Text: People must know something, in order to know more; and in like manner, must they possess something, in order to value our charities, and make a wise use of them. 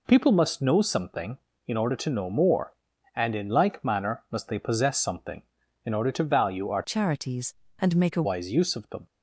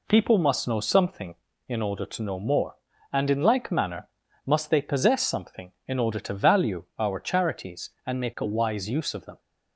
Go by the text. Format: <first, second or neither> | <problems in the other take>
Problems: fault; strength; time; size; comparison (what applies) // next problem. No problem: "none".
second | changes voice from "charities" to "a"; from 6.8 to 8.2 s; 1.4 s long